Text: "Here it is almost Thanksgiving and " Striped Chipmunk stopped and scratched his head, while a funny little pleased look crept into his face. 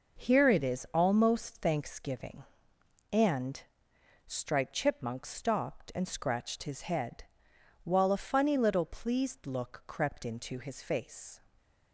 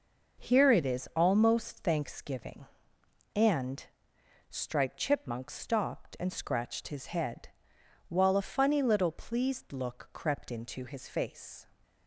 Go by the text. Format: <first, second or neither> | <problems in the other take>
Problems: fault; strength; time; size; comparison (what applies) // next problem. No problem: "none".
neither | none